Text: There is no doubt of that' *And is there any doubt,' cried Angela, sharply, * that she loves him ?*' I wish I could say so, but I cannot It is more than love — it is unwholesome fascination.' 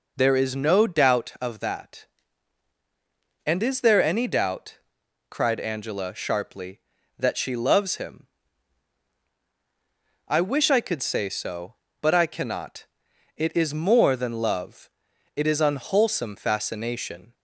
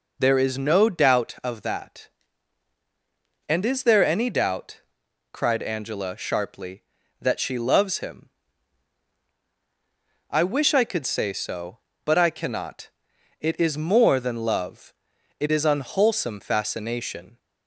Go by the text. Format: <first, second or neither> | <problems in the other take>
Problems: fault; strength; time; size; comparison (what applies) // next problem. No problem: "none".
neither | pauses between "cannot" and "It"; noticeable; the same in both